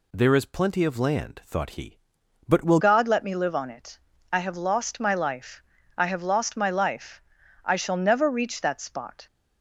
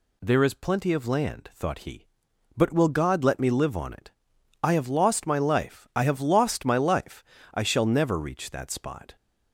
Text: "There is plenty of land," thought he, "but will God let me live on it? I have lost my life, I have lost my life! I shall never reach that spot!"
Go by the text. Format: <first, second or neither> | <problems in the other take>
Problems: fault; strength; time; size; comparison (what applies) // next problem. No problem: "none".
second | changes voice at "God"; from 2.7 s on; 6.5 s long